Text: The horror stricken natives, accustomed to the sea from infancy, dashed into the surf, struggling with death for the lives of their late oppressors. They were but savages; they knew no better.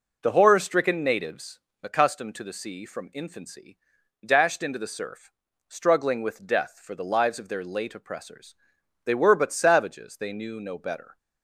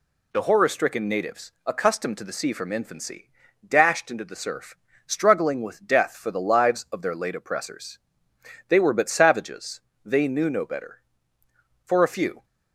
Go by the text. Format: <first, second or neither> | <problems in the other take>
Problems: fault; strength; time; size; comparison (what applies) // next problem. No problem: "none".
first | goes on to say "For a few"; from 11.8 s on; 0.60 s long